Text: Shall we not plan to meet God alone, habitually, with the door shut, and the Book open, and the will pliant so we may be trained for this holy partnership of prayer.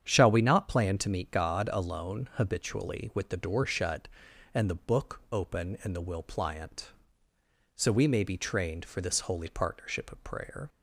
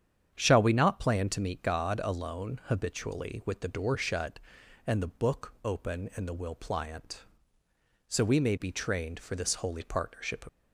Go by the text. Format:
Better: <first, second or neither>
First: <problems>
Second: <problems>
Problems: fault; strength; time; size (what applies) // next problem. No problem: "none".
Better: first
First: starts louder than the rest; strong; until 1.0 s; 8.5 dB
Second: starts louder than the rest; strong; until 1.3 s; 8.5 dB // stops before "of prayer"; at 10.4 s